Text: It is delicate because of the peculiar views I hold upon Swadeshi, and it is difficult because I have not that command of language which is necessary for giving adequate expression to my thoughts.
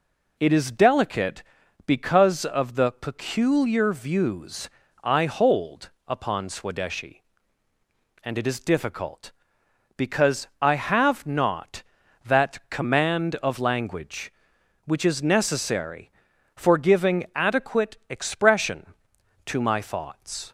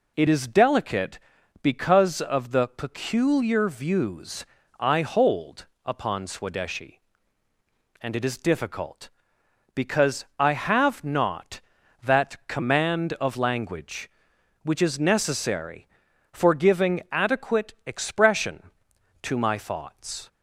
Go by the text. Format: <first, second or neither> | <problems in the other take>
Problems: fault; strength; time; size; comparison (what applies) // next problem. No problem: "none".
neither | pauses between "views" and "I"; slight; the same in both // pauses between "hold" and "upon"; slight; the same in both